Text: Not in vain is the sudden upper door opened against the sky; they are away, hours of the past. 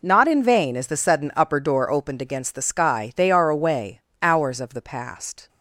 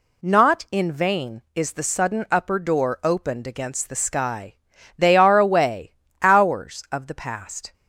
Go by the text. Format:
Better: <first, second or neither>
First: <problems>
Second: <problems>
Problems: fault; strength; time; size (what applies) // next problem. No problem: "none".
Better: neither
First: none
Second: none